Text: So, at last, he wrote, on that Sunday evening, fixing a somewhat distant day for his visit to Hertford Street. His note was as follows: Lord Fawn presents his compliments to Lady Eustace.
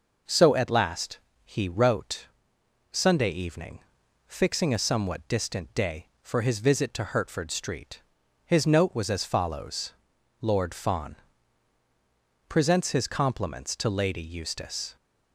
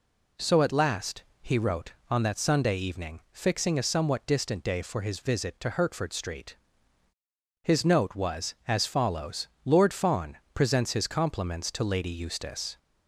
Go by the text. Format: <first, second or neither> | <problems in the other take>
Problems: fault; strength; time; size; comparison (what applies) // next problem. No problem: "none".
second | skips "on that"; at 2.5 s // pauses between "Fawn" and "presents"; strong; at 11.1 s; 1.3 s long; slight in the second